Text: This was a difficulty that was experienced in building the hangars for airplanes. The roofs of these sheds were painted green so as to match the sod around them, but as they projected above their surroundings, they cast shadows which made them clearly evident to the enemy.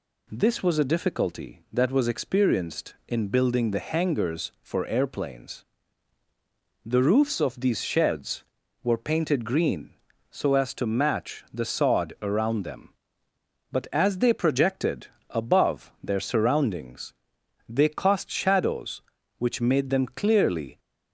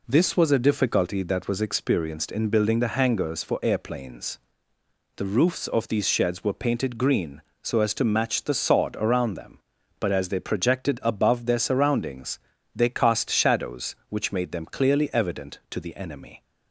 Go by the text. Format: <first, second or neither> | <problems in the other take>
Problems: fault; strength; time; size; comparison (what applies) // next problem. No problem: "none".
second | pauses between "projected" and "above"; slight; at 15.0 s; 0.24 s long // stops before "evident to the enemy"; at 20.7 s